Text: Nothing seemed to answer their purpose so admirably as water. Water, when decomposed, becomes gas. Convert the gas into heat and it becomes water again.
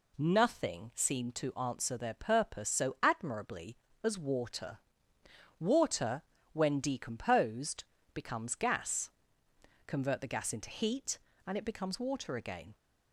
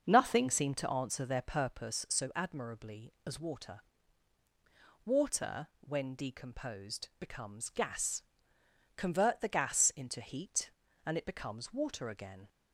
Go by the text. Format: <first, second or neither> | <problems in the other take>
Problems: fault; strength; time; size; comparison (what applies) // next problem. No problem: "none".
first | starts louder than the rest; until 1.9 s; 6.5 dB